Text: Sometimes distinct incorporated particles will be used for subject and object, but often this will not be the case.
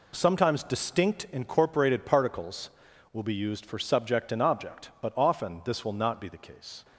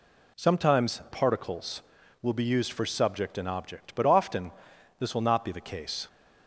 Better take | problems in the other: first | skips "distinct incorporated"; at 1.0 s // pauses between "often" and "this"; noticeable; at 4.5 s; 0.48 s long

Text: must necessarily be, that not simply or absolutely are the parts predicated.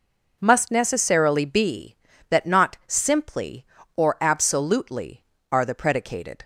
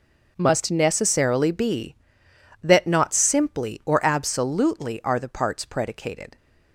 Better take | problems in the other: second | skips "parts"; at 5.7 s

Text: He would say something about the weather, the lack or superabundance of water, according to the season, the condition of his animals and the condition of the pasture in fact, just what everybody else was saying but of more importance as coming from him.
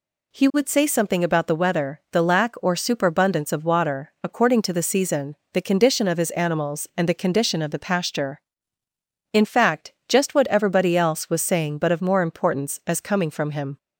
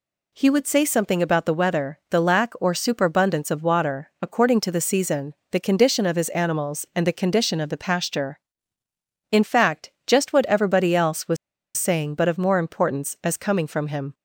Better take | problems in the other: first | pauses between "was" and "saying"; at 11.3 s; 0.41 s long

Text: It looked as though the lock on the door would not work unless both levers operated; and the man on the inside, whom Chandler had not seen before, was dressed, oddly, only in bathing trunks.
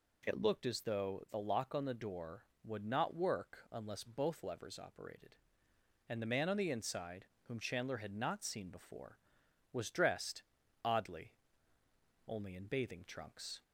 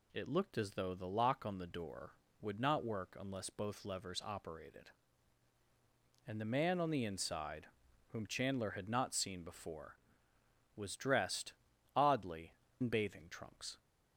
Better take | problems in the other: first | skips "only"; at 12.6 s

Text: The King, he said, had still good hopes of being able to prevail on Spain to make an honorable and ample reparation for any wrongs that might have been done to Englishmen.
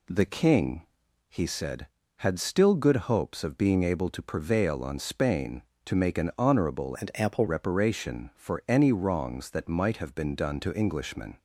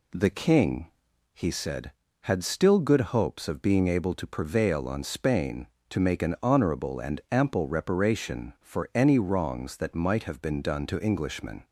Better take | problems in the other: second | changes voice from "and" to "ample"; from 6.9 to 7.4 s; 0.5 s long

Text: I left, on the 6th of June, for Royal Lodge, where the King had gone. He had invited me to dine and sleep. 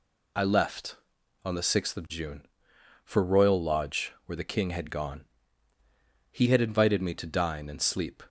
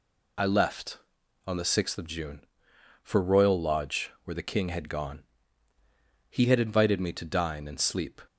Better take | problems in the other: neither | none

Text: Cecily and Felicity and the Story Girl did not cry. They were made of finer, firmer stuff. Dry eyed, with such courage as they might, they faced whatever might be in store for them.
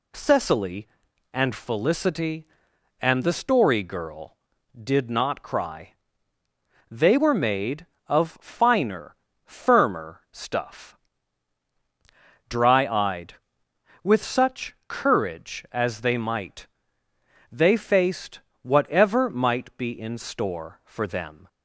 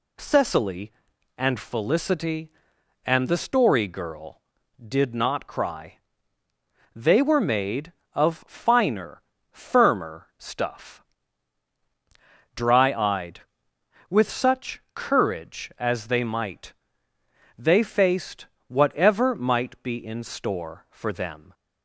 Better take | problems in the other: neither | pauses between "faced" and "whatever"; slight; the same in both

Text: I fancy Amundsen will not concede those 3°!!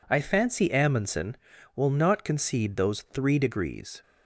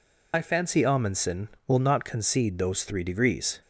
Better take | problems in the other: first | loses the start of "I"; at 0.3 s; 40 ms

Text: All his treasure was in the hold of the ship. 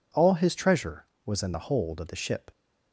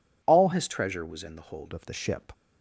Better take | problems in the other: first | changes voice from "his" to "hold"; from 0.5 to 1.7 s; 1.2 s long

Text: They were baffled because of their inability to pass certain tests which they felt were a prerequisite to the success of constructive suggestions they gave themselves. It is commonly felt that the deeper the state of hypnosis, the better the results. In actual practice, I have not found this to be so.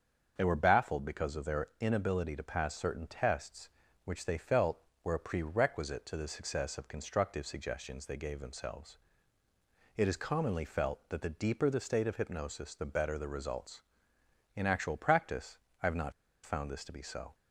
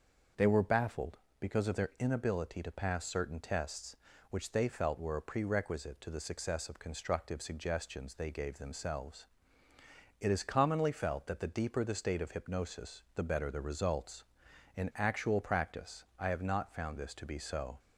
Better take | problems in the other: second | starts louder than the rest; until 1.3 s; 7 dB; also in the second // pauses between "not" and "found"; slight; at 16.1 s; 0.32 s long

